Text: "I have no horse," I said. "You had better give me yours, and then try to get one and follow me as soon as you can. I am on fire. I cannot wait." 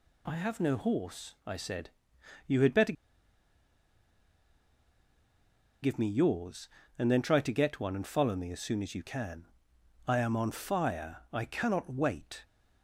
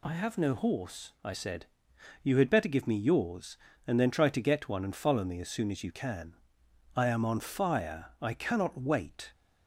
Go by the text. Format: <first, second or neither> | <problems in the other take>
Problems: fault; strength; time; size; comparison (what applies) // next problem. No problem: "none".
second | pauses between "better" and "give"; strong; at 2.9 s; 2.9 s long